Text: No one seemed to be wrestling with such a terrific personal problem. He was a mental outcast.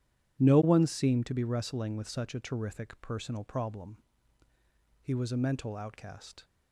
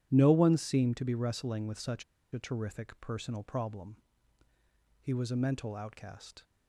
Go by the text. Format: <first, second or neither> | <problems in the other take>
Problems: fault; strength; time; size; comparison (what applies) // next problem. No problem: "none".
first | pauses between "such" and "a"; slight; at 2.0 s; 0.29 s long